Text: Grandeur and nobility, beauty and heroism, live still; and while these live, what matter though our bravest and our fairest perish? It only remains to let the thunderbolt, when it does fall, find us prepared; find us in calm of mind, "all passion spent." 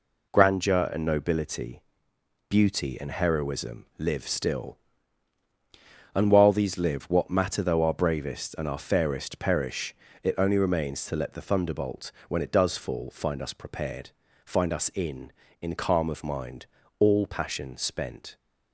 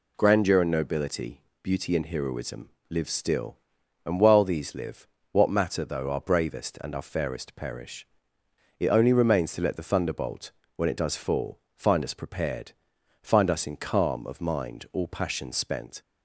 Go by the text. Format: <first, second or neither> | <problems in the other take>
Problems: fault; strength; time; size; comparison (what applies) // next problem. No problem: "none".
second | says "in" twice; at 15.6 s